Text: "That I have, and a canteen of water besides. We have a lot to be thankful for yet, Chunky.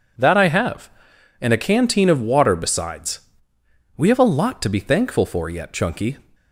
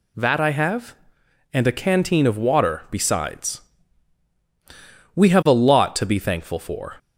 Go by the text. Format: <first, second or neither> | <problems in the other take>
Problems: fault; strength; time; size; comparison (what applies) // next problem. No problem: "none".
first | stops before "yet Chunky"; at 6.9 s